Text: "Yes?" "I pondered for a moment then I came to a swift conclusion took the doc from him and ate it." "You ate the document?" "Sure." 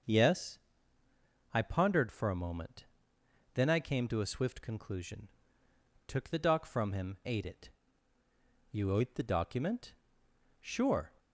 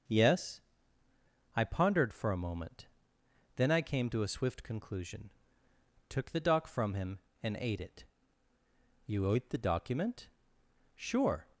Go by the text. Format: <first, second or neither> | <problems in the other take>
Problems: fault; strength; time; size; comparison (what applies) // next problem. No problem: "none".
second | starts louder than the rest; until 2.0 s; 6.5 dB; also in the second // pauses between "moment" and "then"; noticeable; at 2.8 s; 0.70 s long; noticeable in the second // pauses between "conclusion" and "took"; noticeable; at 5.2 s; 0.78 s long; noticeable in the second // skips "and"; at 7.2 s